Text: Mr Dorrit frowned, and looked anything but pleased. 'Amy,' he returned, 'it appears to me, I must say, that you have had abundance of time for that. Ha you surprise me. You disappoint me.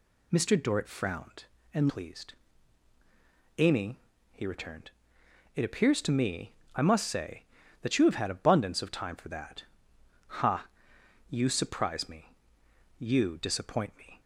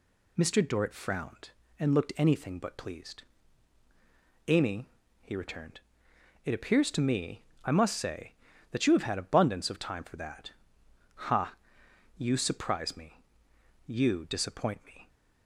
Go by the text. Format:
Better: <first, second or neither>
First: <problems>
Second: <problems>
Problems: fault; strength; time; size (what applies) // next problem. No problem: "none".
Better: second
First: skips "looked anything but"; at 1.8 s // pauses between "Ha" and "you"; noticeable; at 10.6 s; 0.60 s long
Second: pauses between "Ha" and "you"; noticeable; at 11.5 s; 0.60 s long